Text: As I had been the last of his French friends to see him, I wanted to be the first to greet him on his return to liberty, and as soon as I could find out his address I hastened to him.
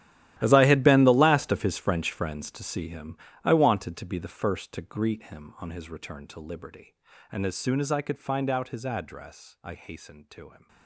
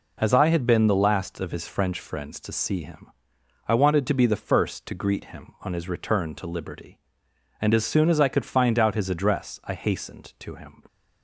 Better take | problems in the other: second | gets quieter; strong; throughout; 17 dB

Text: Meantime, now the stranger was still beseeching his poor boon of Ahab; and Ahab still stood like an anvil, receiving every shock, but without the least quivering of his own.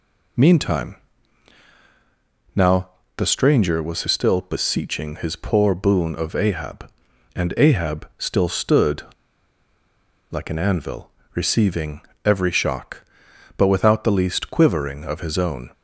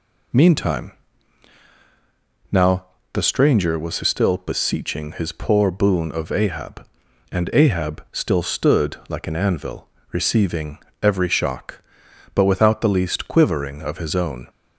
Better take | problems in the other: second | pauses between "now" and "the"; slight; at 2.8 s; 0.28 s long; slight in the second // pauses between "stood" and "like"; strong; at 9.0 s; 1.2 s long // pauses between "receiving" and "every"; slight; at 12.0 s; 0.22 s long; slight in the second

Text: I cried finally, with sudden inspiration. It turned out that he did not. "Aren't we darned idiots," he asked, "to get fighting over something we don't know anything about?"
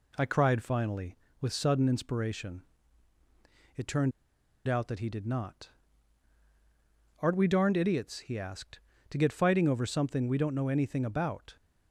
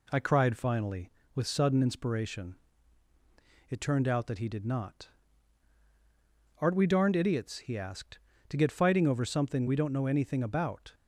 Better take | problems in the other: second | pauses between "turned" and "out"; noticeable; at 4.1 s; 0.56 s long

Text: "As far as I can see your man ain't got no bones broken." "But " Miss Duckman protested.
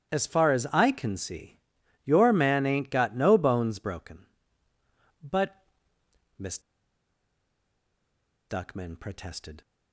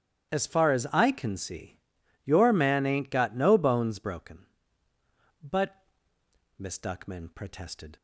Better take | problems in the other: second | starts louder than the rest; strong; until 1.1 s; 11.5 dB; strong in the second // pauses between "see" and "your"; noticeable; at 1.5 s; 0.46 s long; noticeable in the second // pauses between "Miss" and "Duckman"; strong; at 6.5 s; 1.9 s long

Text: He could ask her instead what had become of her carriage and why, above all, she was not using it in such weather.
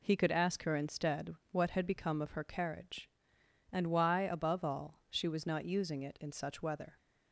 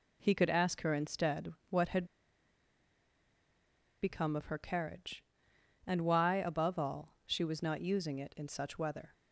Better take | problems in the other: first | pauses between "instead" and "what"; slight; at 1.5 s; 0.20 s long; slight in the first // pauses between "had" and "become"; strong; at 2.0 s; 1.9 s long

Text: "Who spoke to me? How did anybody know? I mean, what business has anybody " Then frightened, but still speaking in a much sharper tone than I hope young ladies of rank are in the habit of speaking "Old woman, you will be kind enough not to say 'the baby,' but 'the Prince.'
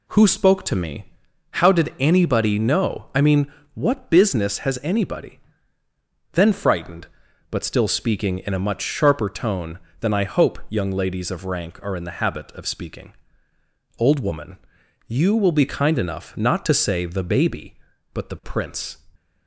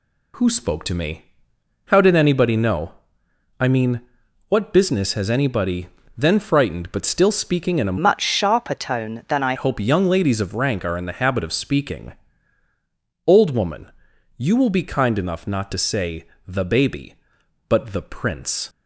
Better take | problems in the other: first | changes voice from "much" to "I"; from 7.9 to 9.5 s; 1.6 s long // pauses between "speaking" and "Old"; at 12.1 s; 1.1 s long; noticeable in the first // pauses between "say" and "the"; slight; at 16.2 s; 0.18 s long

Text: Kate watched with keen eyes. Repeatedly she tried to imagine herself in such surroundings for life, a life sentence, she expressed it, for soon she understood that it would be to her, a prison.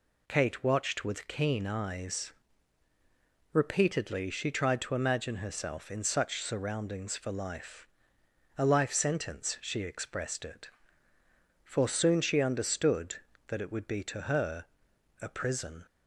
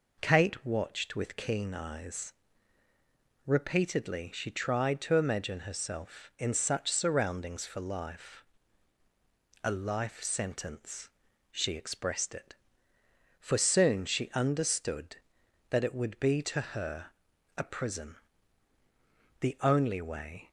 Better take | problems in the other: first | goes on to say "The only way"; noticeable; from 19.3 s on; 1.1 s long

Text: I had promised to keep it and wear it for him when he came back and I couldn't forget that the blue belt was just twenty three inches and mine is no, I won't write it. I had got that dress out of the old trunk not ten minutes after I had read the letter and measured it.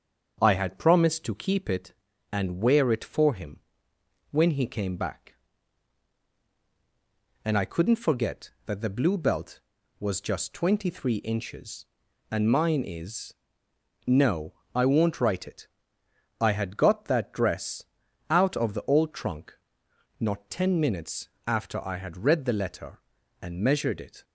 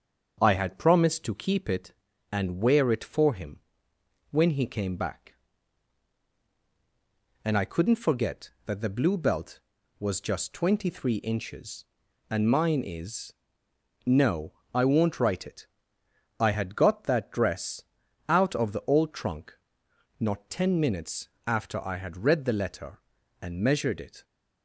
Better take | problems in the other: neither | starts louder than the rest; the same in both // pauses between "him" and "when"; noticeable; the same in both // pauses between "is" and "no"; noticeable; the same in both // pauses between "dress" and "out"; noticeable; the same in both // pauses between "trunk" and "not"; noticeable; the same in both // pauses between "minutes" and "after"; slight; the same in both

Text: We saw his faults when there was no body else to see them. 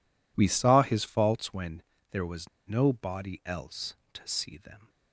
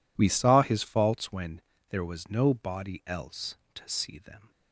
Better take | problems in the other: second | pauses between "when" and "there"; slight; at 1.8 s; 0.30 s long; slight in the second // pauses between "was" and "no"; slight; at 2.4 s; 0.20 s long

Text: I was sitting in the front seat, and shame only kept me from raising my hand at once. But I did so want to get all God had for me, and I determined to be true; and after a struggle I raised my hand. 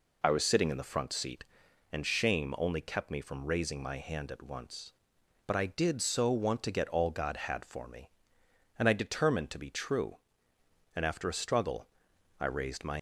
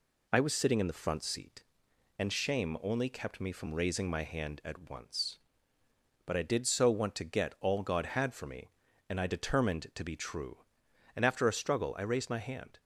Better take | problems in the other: second | pauses between "struggle" and "I"; noticeable; at 11.8 s; 0.52 s long // stops before "hand"; at 12.9 s

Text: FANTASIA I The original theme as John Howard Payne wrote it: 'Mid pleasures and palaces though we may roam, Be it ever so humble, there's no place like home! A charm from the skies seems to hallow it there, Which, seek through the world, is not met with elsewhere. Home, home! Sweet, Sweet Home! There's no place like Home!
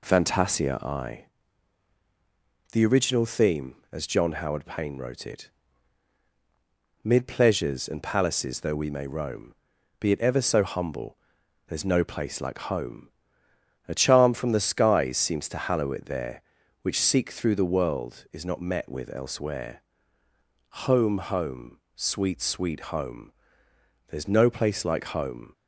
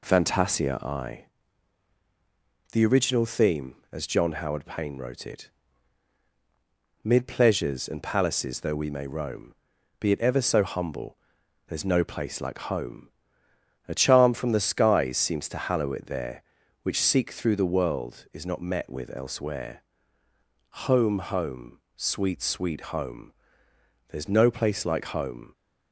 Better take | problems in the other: neither | pauses between "I" and "The"; strong; the same in both

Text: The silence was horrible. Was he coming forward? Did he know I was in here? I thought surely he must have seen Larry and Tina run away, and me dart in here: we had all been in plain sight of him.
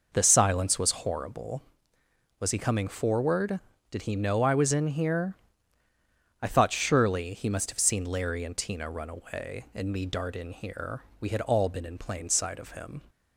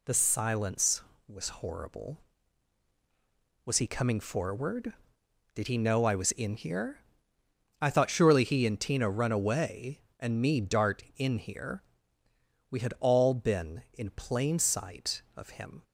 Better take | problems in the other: first | skips "must have seen Larry"; at 8.6 s

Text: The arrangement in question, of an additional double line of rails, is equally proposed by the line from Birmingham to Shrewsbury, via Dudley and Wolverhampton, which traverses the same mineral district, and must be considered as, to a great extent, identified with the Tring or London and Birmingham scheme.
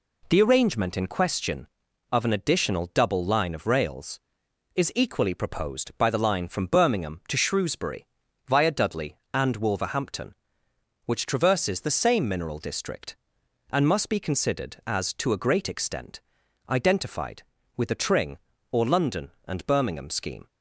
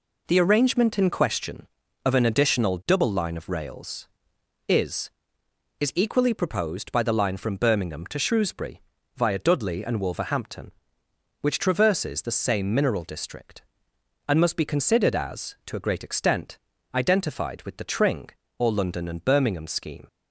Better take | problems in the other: first | says "is" twice; at 5.8 s

